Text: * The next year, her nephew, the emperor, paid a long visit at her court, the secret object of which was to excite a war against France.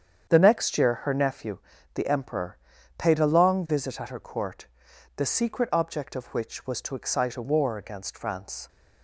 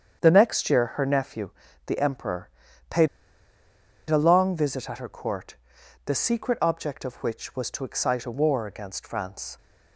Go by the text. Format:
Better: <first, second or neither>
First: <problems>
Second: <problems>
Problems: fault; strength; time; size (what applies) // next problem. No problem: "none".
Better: first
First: starts louder than the rest; strong; until 1.3 s; 8 dB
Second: starts louder than the rest; strong; until 1.2 s; 8 dB // pauses between "paid" and "a"; at 3.0 s; 1.0 s long